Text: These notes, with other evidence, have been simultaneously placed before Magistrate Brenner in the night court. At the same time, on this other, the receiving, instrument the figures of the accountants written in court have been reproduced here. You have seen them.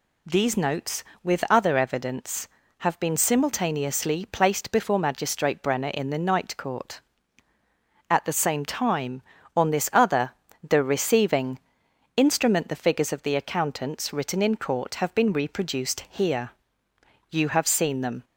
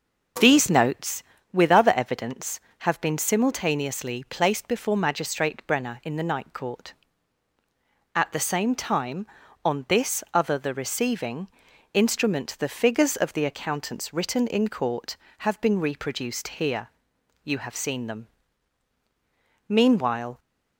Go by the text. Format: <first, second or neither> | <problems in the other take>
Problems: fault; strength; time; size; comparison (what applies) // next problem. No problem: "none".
first | goes on to say "Meanwhile"; noticeable; from 19.6 s on; 0.72 s long